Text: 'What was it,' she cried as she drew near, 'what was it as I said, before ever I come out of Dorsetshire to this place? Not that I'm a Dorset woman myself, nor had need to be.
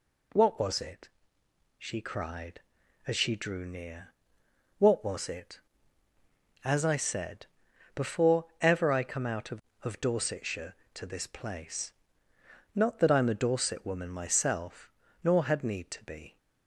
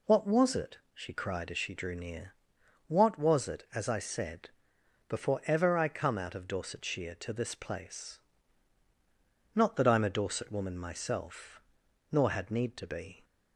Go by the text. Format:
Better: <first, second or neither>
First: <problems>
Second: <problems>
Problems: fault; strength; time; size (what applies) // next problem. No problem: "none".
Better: second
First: pauses between "before" and "ever"; slight; at 8.4 s; 0.16 s long // says "of" twice; at 9.8 s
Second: none